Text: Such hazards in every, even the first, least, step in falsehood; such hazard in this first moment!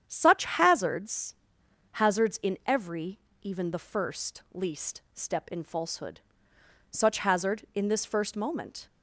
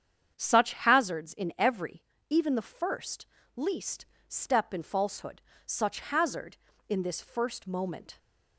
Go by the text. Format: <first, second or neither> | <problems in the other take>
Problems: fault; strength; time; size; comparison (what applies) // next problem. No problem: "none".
second | starts louder than the rest; strong; until 1.0 s; 9 dB; strong in the second // says "hazards" twice; at 1.9 s